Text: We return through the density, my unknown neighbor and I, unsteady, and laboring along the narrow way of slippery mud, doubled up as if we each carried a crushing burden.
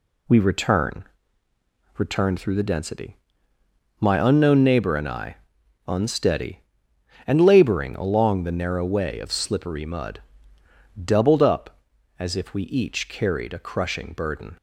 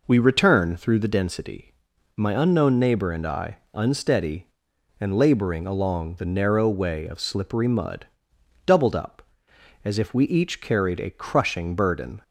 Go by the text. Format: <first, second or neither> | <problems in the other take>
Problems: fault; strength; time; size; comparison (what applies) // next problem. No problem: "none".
second | says "return" twice; at 1.9 s